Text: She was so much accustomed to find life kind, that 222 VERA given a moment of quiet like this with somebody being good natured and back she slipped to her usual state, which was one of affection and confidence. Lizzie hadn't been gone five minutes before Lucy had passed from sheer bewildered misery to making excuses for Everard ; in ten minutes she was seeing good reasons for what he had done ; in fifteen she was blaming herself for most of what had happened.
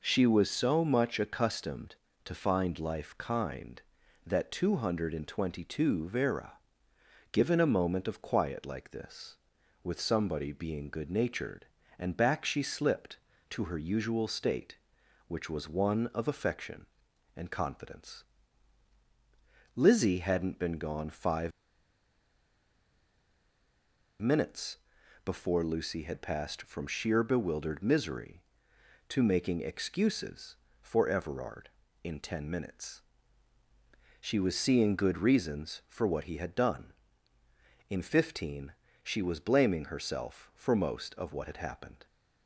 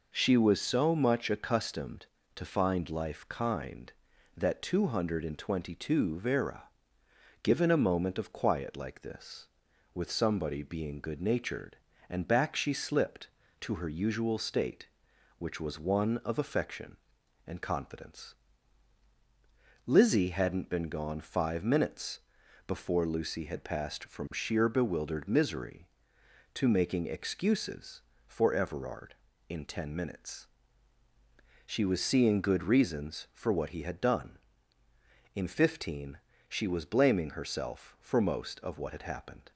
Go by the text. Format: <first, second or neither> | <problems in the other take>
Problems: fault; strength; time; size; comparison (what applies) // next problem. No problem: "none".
second | pauses between "VERA" and "given"; noticeable; at 6.5 s; 0.78 s long; noticeable in the second // pauses between "five" and "minutes"; strong; at 21.5 s; 2.7 s long // pauses between "minutes" and "before"; noticeable; at 24.7 s; 0.46 s long; noticeable in the second // pauses between "minutes" and "she"; at 33.0 s; 1.2 s long; also in the second // pauses between "fifteen" and "she"; slight; at 38.7 s; 0.32 s long; slight in the second